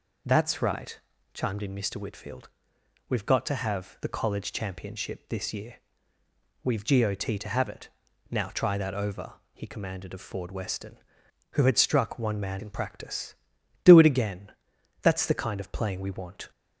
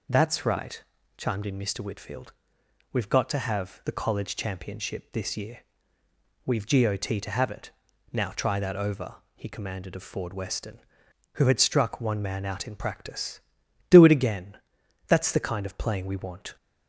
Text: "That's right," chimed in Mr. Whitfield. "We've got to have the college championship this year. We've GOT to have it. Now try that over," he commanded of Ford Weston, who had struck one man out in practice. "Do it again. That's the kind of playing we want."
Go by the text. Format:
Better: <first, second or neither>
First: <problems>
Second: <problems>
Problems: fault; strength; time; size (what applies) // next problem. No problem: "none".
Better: second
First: skips "out"; at 12.6 s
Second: none